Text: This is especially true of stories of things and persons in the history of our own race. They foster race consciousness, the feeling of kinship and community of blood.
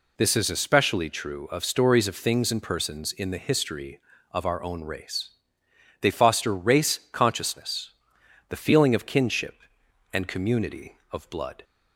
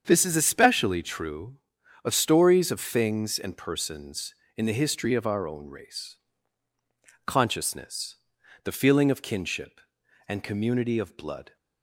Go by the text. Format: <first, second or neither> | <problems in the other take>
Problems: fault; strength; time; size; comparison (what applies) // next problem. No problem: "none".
first | starts louder than the rest; strong; until 1.0 s; 7.5 dB // skips "They foster race"; at 6.7 s